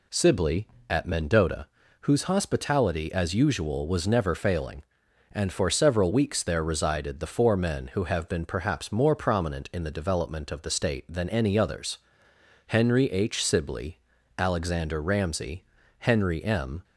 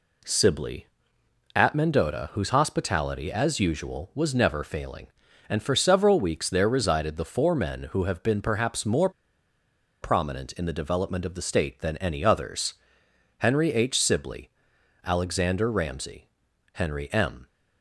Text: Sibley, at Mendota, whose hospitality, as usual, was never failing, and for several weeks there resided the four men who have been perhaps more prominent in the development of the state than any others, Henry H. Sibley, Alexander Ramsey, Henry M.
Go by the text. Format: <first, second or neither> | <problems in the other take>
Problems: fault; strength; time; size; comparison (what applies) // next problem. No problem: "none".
first | pauses between "more" and "prominent"; noticeable; at 9.0 s; 0.92 s long